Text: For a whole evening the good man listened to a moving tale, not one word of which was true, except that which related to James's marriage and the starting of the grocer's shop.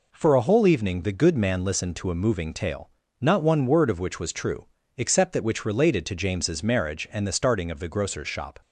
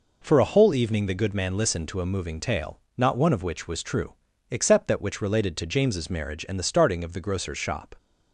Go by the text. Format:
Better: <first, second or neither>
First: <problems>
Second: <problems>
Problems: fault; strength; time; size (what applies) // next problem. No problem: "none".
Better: first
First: none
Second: skips "word"; at 3.3 s